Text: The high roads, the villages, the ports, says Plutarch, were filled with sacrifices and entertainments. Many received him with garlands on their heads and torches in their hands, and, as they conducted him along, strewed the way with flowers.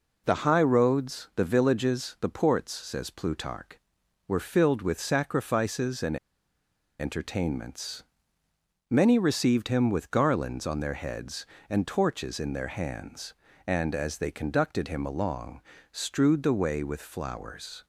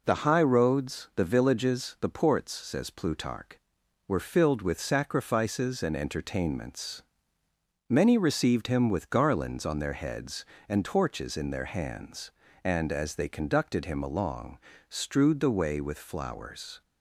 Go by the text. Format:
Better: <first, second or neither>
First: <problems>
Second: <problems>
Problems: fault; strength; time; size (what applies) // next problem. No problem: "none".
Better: second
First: pauses between "and" and "entertainments"; noticeable; at 6.1 s; 0.83 s long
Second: none